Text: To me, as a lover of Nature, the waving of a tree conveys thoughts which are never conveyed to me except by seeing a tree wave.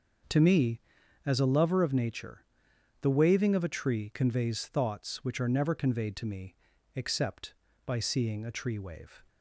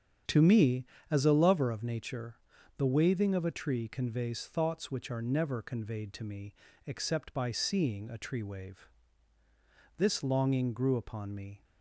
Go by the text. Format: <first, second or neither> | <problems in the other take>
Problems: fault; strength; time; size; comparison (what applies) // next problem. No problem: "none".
first | starts louder than the rest; strong; until 1.5 s; 8.5 dB; also in the first // pauses between "me" and "except"; slight; at 6.5 s; 0.32 s long; also in the first // goes on to say "This longing grew upon me"; from 9.9 s on; 1.6 s long